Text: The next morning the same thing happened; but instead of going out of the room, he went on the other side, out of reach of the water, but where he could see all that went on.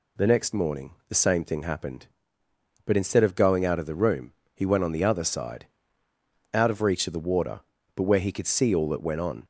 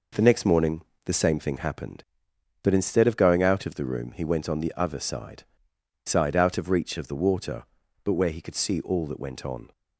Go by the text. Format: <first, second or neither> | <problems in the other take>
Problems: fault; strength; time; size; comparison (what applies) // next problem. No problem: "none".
first | pauses between "morning" and "the"; slight; at 0.8 s; 0.22 s long // says "side" twice; at 6.0 s